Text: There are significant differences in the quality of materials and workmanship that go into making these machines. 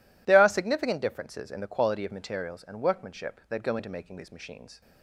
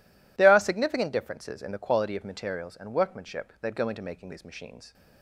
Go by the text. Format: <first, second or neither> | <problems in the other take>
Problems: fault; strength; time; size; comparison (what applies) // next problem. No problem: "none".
neither | none